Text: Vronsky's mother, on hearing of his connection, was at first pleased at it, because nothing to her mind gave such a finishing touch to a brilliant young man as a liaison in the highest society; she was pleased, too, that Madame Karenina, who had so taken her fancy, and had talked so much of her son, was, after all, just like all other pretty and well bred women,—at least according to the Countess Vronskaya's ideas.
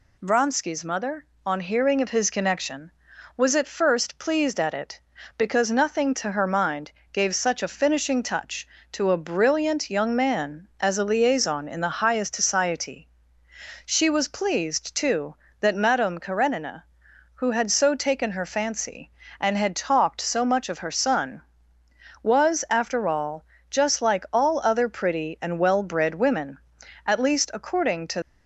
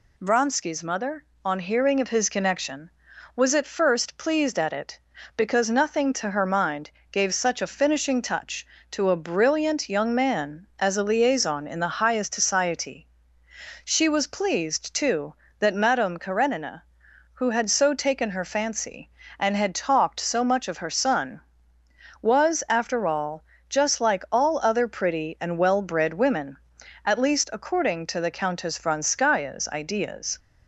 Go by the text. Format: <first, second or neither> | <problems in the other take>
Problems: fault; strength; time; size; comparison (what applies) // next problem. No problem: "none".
second | pauses between "mind" and "gave"; slight; at 6.8 s; 0.22 s long; slight in the second // stops before "the Countess Vronskaya's ideas"; at 28.2 s